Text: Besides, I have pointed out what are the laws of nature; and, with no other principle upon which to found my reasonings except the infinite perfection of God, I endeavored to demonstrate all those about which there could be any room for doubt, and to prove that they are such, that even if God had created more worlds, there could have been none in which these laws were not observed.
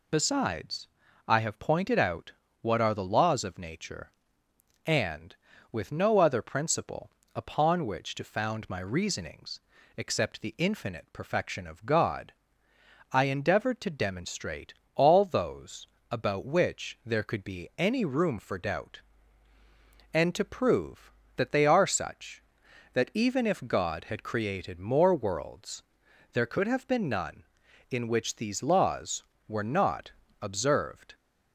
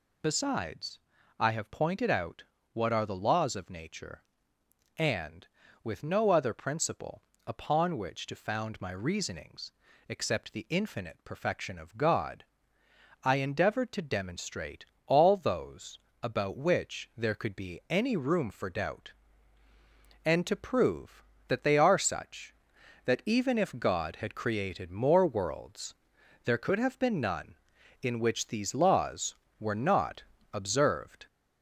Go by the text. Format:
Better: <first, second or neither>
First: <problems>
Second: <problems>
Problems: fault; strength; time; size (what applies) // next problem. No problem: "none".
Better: first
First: pauses between "out" and "what"; slight; at 2.3 s; 0.30 s long // pauses between "principle" and "upon"; slight; at 7.1 s; 0.24 s long // pauses between "reasonings" and "except"; at 9.6 s; 0.38 s long // pauses between "demonstrate" and "all"; slight; at 14.7 s; 0.22 s long // pauses between "those" and "about"; slight; at 15.8 s; 0.24 s long // pauses between "not" and "observed"; slight; at 30.1 s; 0.32 s long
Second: gets louder; throughout; 3.5 dB // pauses between "out" and "what"; slight; at 2.4 s; 0.30 s long // pauses between "principle" and "upon"; slight; at 7.2 s; 0.24 s long // pauses between "reasonings" and "except"; at 9.7 s; 0.38 s long // pauses between "demonstrate" and "all"; slight; at 14.8 s; 0.22 s long // pauses between "those" and "about"; slight; at 15.9 s; 0.24 s long // pauses between "not" and "observed"; slight; at 30.2 s; 0.32 s long